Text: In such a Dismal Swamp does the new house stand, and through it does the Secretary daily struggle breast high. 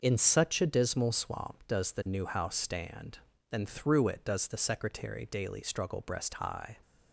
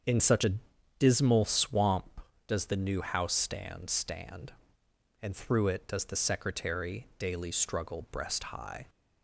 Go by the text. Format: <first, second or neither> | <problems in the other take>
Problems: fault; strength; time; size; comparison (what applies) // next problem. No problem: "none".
first | starts louder than the rest; until 1.5 s; 7 dB; noticeable in the first // pauses between "a" and "Dismal"; at 0.5 s; 0.44 s long // says "stand" twice; at 3.8 s